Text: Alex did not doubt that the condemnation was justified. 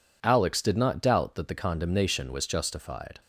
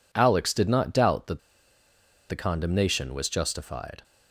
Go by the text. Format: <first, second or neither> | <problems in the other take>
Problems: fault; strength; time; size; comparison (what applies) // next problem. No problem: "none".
first | pauses between "that" and "the"; noticeable; at 1.3 s; 0.89 s long